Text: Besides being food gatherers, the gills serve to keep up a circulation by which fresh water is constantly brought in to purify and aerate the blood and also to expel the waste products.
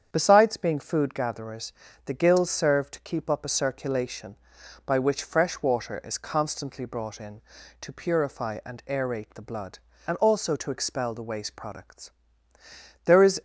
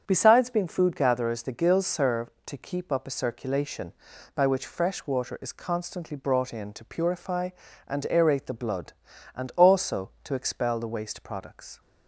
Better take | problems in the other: second | starts louder than the rest; strong; until 1.1 s; 8 dB; strong in the second // goes on to say "There is"; slight; from 13.0 s on; 0.36 s long

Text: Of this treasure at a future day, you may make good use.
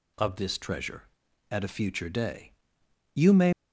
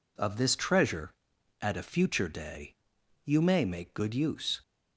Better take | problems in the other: second | stops before "make good use"; at 3.5 s

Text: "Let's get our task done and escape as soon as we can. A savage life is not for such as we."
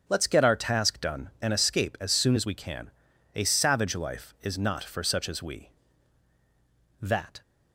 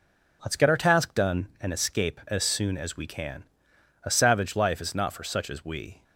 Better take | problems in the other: second | starts louder than the rest; until 1.0 s; 6.5 dB // goes on to say "That"; slight; from 7.0 s on; 0.40 s long

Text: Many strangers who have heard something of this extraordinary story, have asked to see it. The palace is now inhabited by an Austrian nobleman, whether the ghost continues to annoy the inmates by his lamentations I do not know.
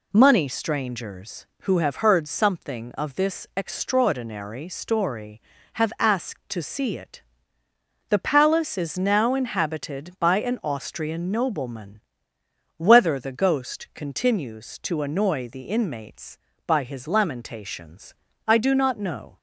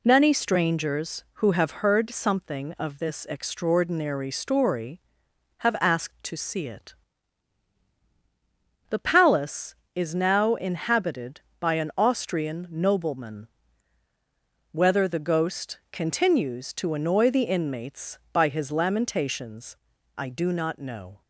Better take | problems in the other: second | says "Money" for "Many"; at 0.1 s // pauses between "lamentations" and "I"; slight; at 18.1 s; 0.32 s long; also in the second

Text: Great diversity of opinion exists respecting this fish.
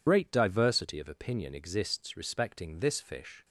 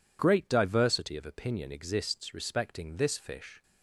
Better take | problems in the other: second | loses the start of "Great"; at 0.0 s; 50 ms

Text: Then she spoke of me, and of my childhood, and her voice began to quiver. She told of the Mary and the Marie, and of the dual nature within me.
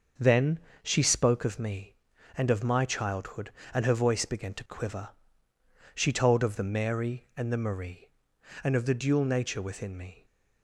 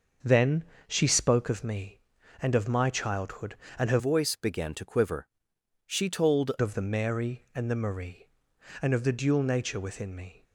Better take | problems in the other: first | starts louder than the rest; noticeable; until 1.4 s; 6 dB; noticeable in the first // pauses between "Then" and "she"; slight; at 0.6 s; 0.22 s long; slight in the first // changes voice from "voice" to "told"; from 3.9 to 6.5 s; 2.6 s long

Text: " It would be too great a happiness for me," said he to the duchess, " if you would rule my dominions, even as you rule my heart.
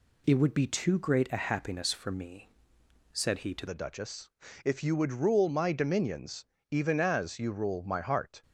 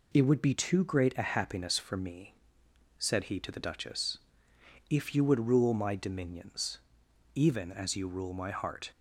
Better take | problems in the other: second | changes voice at "the"; from 3.6 s on; 4.8 s long

